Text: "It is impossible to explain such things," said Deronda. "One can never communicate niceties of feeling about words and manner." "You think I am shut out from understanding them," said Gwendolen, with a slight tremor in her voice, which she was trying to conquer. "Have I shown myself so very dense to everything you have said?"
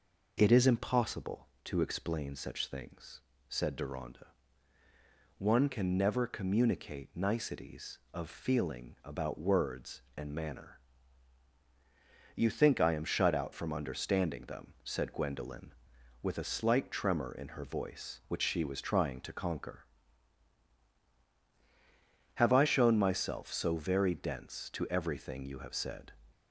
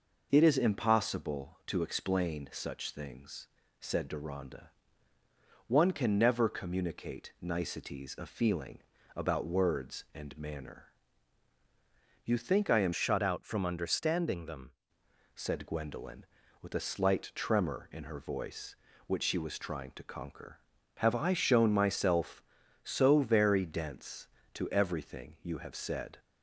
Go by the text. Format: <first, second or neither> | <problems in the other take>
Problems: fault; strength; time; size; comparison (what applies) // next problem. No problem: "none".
first | pauses between "feeling" and "about"; slight; at 8.8 s; 0.36 s long // changes voice from "shut" to "them"; from 12.9 to 14.7 s; 1.8 s long